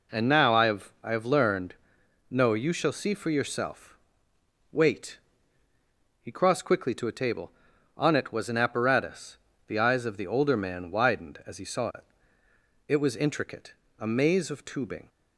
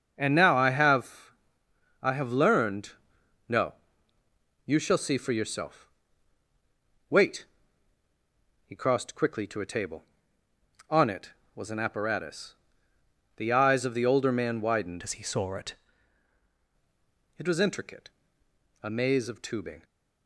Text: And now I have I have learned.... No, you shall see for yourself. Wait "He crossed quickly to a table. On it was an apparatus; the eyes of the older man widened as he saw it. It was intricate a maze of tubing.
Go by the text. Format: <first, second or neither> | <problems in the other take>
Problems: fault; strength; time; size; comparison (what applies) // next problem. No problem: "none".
first | starts louder than the rest; until 1.1 s; 6.5 dB // pauses between "have" and "I"; noticeable; at 1.3 s; 0.70 s long // pauses between "Wait" and "He"; at 7.4 s; 1.2 s long; also in the first // changes voice from "as" to "it"; from 15.0 to 15.7 s; 0.7 s long // pauses between "intricate" and "a"; noticeable; at 18.0 s; 0.72 s long; slight in the first